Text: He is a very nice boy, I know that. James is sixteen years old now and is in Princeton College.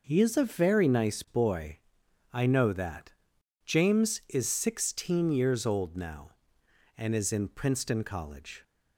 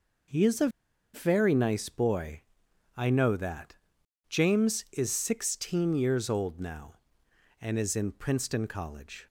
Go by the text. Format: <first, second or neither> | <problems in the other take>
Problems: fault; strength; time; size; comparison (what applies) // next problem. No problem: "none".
first | pauses between "a" and "very"; at 0.6 s; 0.45 s long